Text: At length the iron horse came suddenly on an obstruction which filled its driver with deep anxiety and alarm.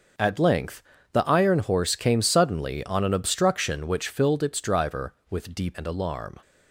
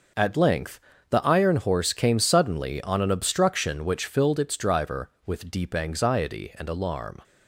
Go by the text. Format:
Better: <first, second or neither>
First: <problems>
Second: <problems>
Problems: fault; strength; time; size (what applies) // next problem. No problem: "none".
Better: second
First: starts louder than the rest; noticeable; until 1.4 s; 6 dB // pauses between "length" and "the"; slight; at 0.8 s; 0.30 s long // skips "anxiety"; at 5.7 s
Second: pauses between "length" and "the"; slight; at 0.7 s; 0.30 s long